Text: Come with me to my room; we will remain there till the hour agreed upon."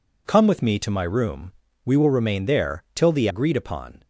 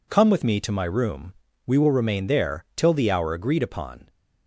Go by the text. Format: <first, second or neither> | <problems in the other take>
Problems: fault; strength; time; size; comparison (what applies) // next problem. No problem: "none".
second | skips "hour"; at 3.2 s